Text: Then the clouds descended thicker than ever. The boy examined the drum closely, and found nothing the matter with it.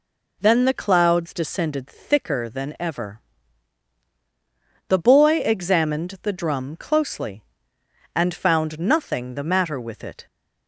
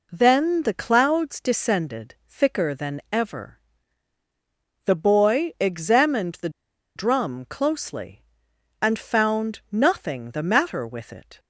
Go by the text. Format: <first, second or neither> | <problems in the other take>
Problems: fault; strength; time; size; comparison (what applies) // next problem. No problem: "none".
first | pauses between "the" and "drum"; noticeable; at 6.4 s; 0.46 s long